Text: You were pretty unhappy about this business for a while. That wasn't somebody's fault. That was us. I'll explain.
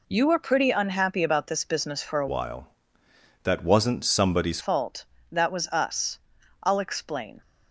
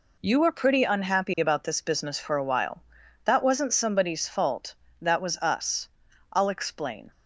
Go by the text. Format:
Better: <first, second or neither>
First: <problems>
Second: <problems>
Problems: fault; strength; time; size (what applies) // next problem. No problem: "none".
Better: second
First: changes voice from "while" to "somebody's"; from 2.2 to 4.6 s; 2.4 s long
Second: none